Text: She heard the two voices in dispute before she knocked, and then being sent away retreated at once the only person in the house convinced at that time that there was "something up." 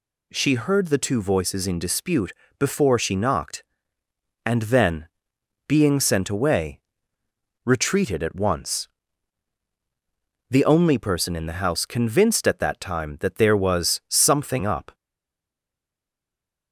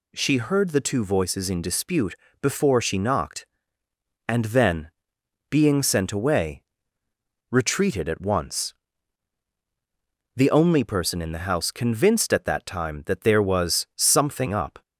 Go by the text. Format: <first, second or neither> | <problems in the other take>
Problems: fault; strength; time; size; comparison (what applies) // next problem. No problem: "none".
second | pauses between "dispute" and "before"; slight; at 2.3 s; 0.26 s long; slight in the second // pauses between "then" and "being"; noticeable; at 5.0 s; 0.60 s long; noticeable in the second // pauses between "away" and "retreated"; noticeable; at 6.7 s; 0.84 s long; noticeable in the second // pauses between "once" and "the"; strong; at 8.8 s; 1.6 s long; strong in the second // stays silent after the last word; noticeable; from 14.9 s on; 1.8 s long